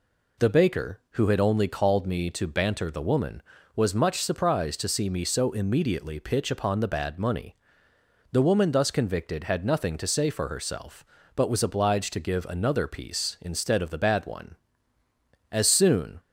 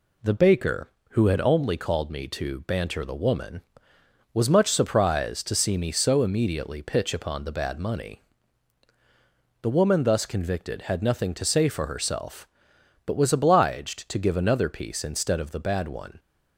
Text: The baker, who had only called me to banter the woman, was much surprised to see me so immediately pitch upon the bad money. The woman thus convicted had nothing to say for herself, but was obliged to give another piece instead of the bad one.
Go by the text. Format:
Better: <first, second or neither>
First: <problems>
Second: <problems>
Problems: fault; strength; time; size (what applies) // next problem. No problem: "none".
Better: second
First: goes on to say "As soon"; noticeable; from 15.5 s on; 0.68 s long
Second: none